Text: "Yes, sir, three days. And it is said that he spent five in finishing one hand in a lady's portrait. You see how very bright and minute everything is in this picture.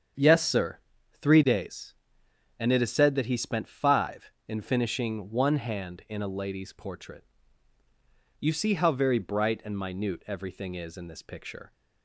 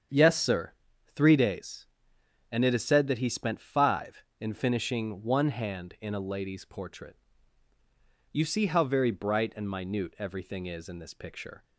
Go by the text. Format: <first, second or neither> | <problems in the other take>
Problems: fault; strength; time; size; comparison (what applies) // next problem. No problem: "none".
neither | starts louder than the rest; strong; the same in both